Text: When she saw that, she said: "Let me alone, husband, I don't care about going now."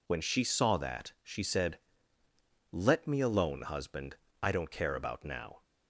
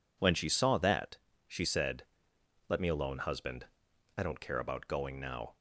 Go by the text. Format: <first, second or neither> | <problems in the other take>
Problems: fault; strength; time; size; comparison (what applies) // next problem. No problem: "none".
second | skips "going"; at 5.2 s